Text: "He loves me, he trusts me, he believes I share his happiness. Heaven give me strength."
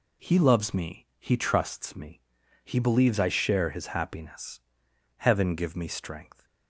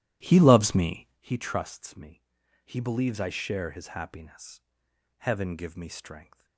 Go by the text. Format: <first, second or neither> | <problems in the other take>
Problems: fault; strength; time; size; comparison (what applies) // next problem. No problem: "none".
first | starts louder than the rest; strong; until 1.2 s; 13.5 dB